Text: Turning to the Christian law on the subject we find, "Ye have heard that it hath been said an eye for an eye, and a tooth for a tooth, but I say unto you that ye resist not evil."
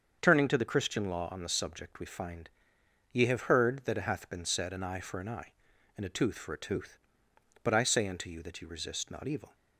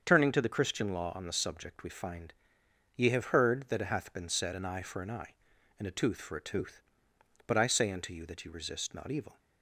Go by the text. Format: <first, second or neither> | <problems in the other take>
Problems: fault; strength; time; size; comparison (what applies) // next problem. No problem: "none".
neither | starts louder than the rest; the same in both